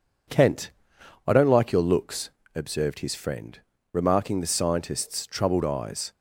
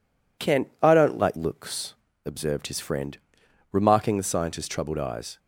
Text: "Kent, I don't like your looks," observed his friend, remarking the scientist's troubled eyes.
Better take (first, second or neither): first